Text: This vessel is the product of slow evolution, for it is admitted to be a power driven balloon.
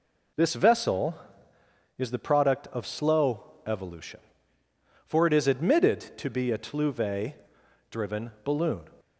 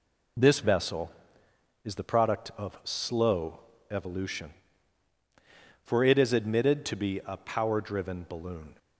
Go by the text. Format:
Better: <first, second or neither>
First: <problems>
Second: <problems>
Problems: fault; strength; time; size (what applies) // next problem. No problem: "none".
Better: second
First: pauses between "slow" and "evolution"; slight; at 3.4 s; 0.24 s long // says "tluve" for "power"; at 6.5 s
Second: pauses between "slow" and "evolution"; slight; at 3.5 s; 0.32 s long